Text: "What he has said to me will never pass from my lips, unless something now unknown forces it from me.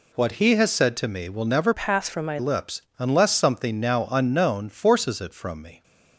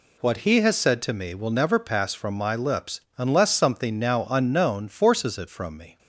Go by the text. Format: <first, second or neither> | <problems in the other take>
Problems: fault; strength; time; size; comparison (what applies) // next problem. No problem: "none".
second | changes voice from "pass" to "my"; from 1.7 to 2.3 s; 0.6 s long